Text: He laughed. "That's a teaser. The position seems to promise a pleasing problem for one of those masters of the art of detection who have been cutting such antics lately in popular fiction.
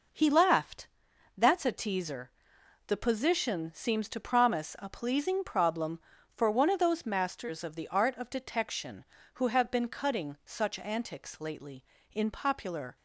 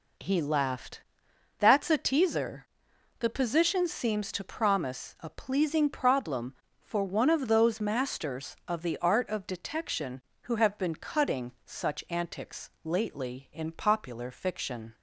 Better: second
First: stops before "fiction"; at 12.9 s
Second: none

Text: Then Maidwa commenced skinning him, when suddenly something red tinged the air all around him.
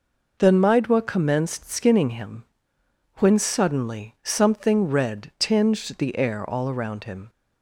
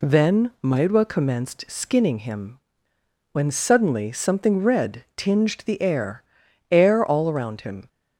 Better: first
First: none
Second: says "air" twice; at 6.7 s

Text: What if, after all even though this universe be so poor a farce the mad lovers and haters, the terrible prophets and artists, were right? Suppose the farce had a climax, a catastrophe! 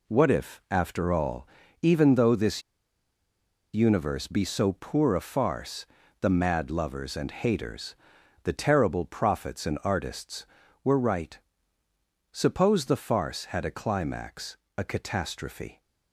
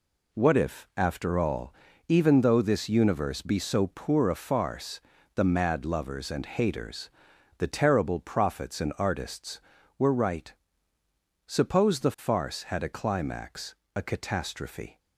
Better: second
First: pauses between "all" and "even"; slight; at 1.4 s; 0.34 s long // pauses between "this" and "universe"; at 2.6 s; 1.1 s long // pauses between "farce" and "the"; slight; at 5.8 s; 0.36 s long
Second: pauses between "all" and "even"; slight; at 1.7 s; 0.34 s long // pauses between "farce" and "the"; slight; at 4.9 s; 0.36 s long

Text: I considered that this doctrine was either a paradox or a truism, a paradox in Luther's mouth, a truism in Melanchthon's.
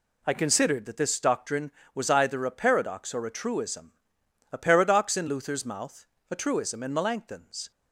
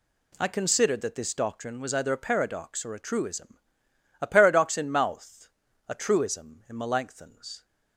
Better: first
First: none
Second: skips "Luther's"; at 4.8 s

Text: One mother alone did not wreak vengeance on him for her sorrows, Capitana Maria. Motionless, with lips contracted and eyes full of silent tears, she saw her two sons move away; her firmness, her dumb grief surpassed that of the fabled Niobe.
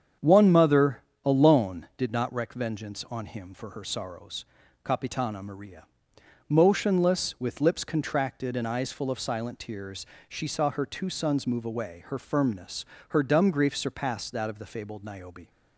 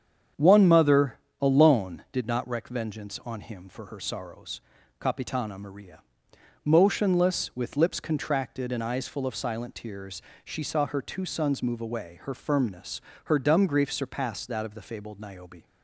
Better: neither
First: starts louder than the rest; strong; until 1.4 s; 7.5 dB // pauses between "mother" and "alone"; slight; at 1.0 s; 0.22 s long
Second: starts louder than the rest; strong; until 1.5 s; 7.5 dB // pauses between "mother" and "alone"; slight; at 1.1 s; 0.22 s long

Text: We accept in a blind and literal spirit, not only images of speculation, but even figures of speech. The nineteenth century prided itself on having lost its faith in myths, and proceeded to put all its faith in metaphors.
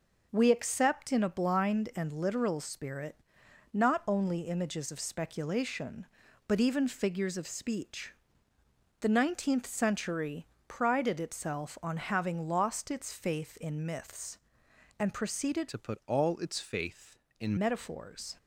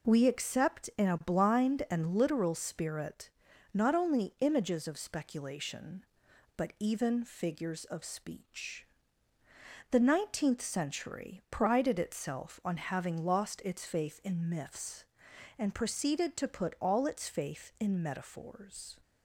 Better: second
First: pauses between "century" and "prided"; slight; at 10.4 s; 0.22 s long // changes voice from "to" to "in"; from 15.6 to 17.5 s; 1.9 s long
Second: none

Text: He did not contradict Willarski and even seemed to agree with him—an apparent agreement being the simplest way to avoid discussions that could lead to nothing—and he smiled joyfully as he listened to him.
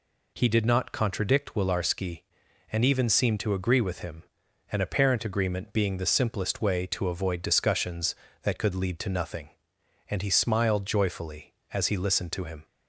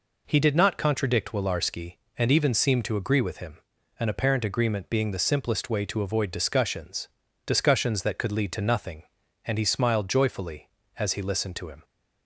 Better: first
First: none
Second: says "discussions" twice; at 7.4 s

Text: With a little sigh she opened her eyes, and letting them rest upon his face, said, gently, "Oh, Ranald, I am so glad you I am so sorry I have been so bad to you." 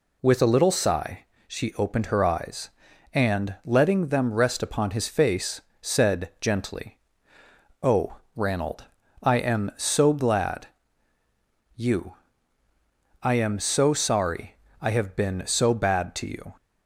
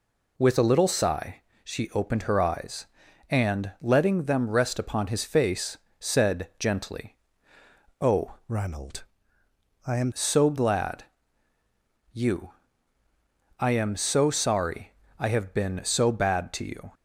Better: first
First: pauses between "sigh" and "she"; slight; at 1.2 s; 0.22 s long // pauses between "glad" and "you"; at 10.6 s; 1.0 s long // pauses between "you" and "I"; at 12.1 s; 1.0 s long // pauses between "sorry" and "I"; slight; at 14.5 s; 0.27 s long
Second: pauses between "sigh" and "she"; slight; at 1.4 s; 0.22 s long // changes voice from "Ranald" to "am"; from 8.4 to 10.1 s; 1.7 s long // pauses between "glad" and "you"; at 11.0 s; 1.0 s long // pauses between "you" and "I"; at 12.5 s; 1.0 s long // pauses between "sorry" and "I"; slight; at 14.9 s; 0.28 s long

